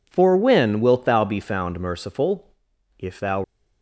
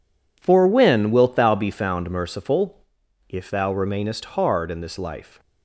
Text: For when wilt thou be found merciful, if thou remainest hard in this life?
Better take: second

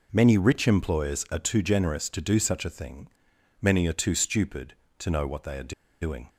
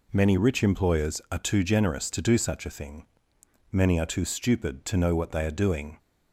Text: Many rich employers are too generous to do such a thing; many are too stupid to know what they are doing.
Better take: second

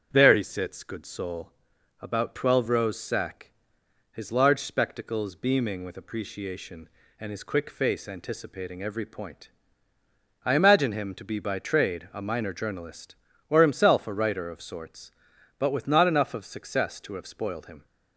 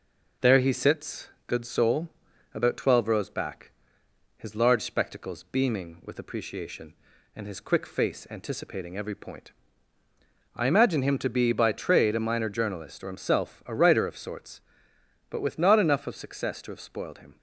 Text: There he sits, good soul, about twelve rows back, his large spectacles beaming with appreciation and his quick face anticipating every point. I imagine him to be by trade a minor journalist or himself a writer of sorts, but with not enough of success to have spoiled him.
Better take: second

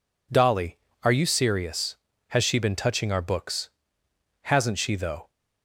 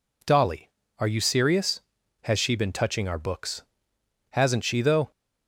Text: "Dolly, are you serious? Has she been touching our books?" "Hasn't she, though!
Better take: neither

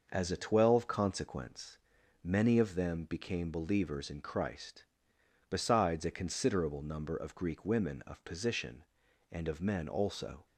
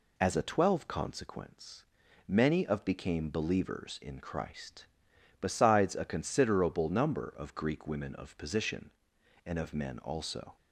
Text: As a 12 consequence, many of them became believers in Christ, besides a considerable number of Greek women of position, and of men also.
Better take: first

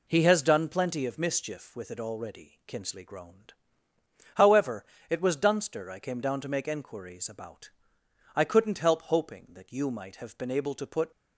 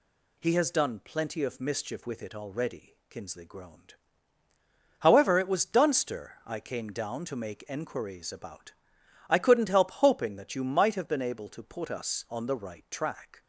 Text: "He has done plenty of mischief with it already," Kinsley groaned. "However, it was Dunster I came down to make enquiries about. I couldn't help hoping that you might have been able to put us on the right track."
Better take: second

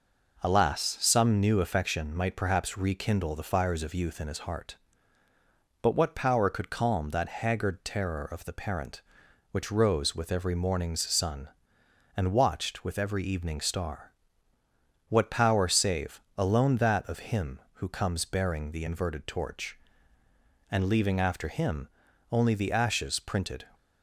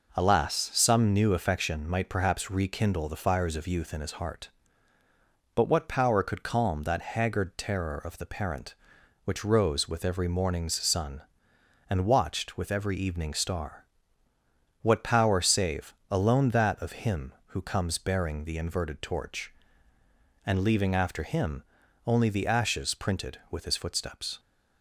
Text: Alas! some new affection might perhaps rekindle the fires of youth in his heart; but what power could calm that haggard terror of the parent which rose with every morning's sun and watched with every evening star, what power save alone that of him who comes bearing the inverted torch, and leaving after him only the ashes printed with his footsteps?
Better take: second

